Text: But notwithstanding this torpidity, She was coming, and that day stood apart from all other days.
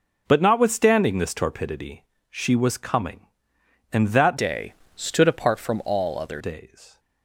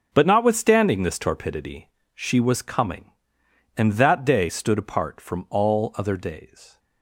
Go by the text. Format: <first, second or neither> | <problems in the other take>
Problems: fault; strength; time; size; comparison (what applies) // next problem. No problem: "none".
second | changes voice from "day" to "other"; from 4.3 to 6.4 s; 2.1 s long // pauses between "day" and "stood"; slight; at 4.7 s; 0.24 s long